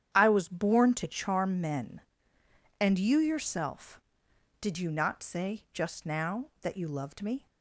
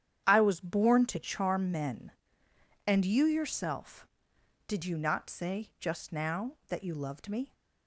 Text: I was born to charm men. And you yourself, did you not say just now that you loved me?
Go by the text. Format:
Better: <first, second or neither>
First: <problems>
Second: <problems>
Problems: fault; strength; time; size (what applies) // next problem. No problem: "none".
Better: neither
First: starts louder than the rest; strong; until 1.1 s; 9.5 dB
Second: starts louder than the rest; strong; until 1.2 s; 9.5 dB